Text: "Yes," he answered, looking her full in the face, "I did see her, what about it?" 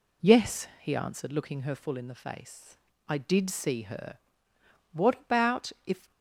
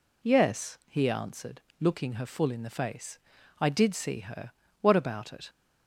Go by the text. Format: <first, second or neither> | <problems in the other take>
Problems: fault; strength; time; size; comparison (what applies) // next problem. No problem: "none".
second | says "if" for "it"; at 5.8 s